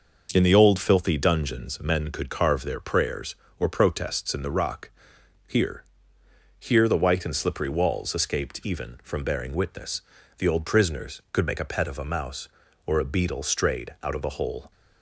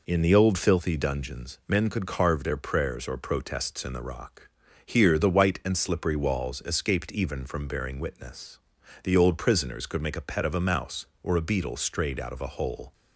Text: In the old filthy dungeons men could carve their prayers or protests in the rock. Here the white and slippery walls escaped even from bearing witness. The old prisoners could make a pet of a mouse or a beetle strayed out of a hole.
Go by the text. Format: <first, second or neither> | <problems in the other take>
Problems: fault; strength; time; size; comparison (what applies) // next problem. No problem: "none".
second | says "Here" twice; at 6.5 s